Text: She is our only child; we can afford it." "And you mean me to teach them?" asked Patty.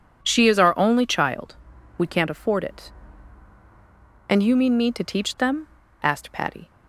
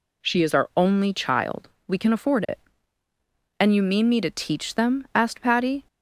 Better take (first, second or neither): second